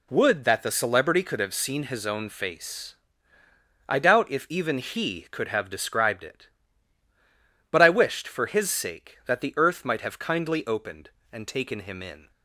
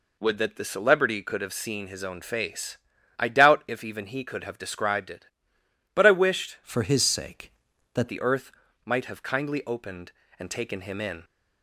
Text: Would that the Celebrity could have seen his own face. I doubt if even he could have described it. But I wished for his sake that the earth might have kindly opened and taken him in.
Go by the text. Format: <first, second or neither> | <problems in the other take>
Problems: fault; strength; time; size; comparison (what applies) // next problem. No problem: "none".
first | changes voice from "for" to "that"; from 6.6 to 8.0 s; 1.4 s long // pauses between "earth" and "might"; slight; at 8.5 s; 0.32 s long